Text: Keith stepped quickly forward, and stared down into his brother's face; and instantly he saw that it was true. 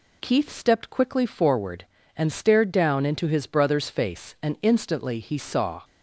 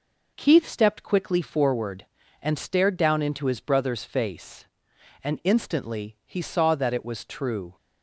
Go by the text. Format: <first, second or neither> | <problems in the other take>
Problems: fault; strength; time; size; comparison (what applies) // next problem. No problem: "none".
second | stops before "that it was true"; at 5.8 s